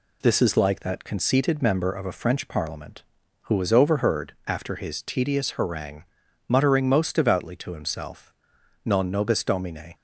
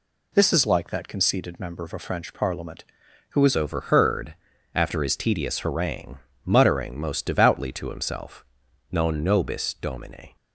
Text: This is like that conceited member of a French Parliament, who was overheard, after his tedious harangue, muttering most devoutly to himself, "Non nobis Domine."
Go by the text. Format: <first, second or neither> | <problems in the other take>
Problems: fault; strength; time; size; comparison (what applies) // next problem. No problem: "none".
first | changes voice at "overheard"; from 3.5 s on; 6.8 s long